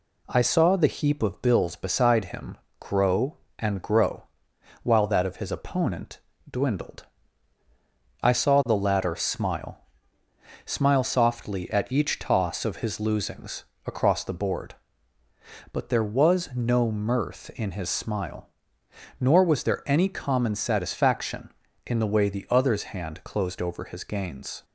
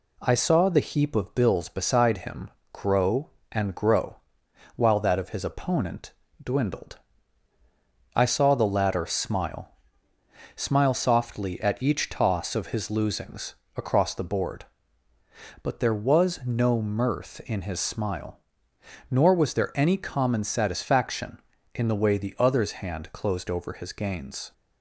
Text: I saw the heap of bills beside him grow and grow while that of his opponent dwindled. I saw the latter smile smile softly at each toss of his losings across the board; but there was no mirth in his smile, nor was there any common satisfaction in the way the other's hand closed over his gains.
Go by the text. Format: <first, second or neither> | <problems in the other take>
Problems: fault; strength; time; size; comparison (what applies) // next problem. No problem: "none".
neither | pauses between "him" and "grow"; slight; the same in both // pauses between "grow" and "while"; noticeable; the same in both // pauses between "opponent" and "dwindled"; slight; the same in both // pauses between "smile" and "smile"; noticeable; the same in both // pauses between "losings" and "across"; slight; the same in both